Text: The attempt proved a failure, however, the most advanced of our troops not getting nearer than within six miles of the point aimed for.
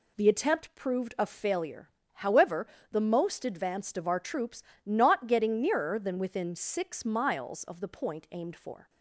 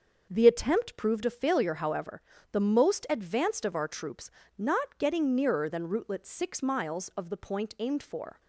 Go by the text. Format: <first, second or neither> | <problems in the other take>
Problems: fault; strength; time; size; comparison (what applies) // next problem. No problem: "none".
first | starts louder than the rest; until 1.3 s; 6.5 dB // pauses between "troops" and "not"; slight; at 4.2 s; 0.28 s long; slight in the first // says "rootlet" for "within"; at 5.8 s